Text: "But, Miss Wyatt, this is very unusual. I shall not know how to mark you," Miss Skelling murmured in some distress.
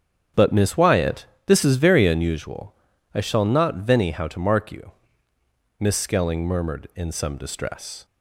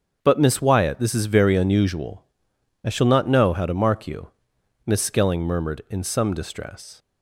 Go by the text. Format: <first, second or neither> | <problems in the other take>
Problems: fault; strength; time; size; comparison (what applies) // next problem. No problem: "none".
second | starts louder than the rest; strong; until 1.5 s; 8 dB; also in the second // says "venny" for "know"; at 3.8 s